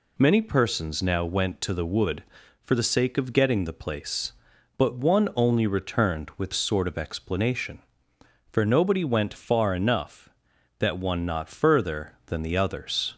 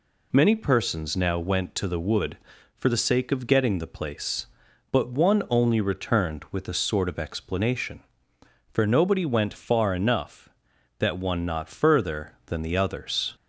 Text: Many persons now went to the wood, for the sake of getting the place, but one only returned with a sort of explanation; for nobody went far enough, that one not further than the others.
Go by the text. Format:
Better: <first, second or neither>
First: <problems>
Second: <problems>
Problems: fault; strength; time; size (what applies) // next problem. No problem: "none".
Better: second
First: skips "a"; at 6.5 s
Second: none